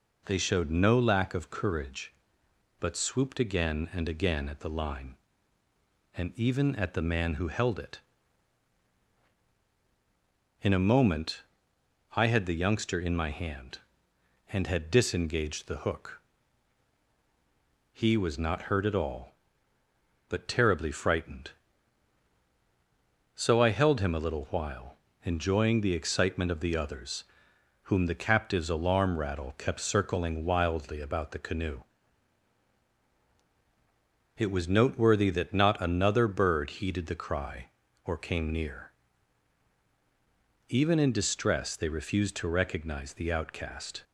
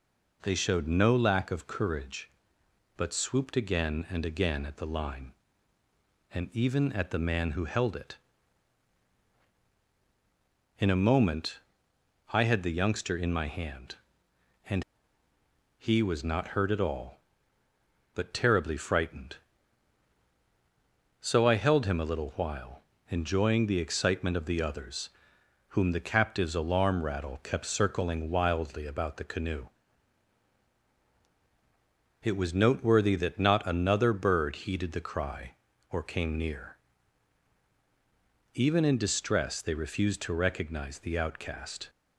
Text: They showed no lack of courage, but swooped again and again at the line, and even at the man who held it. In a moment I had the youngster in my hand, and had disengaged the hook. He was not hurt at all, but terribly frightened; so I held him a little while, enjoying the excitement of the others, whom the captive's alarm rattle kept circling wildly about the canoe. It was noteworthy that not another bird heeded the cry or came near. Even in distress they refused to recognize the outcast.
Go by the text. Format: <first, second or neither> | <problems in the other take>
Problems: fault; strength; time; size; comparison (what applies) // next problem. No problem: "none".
first | pauses between "moment" and "I"; noticeable; at 11.5 s; 0.72 s long; noticeable in the first // skips "had disengaged the hook"; at 15.2 s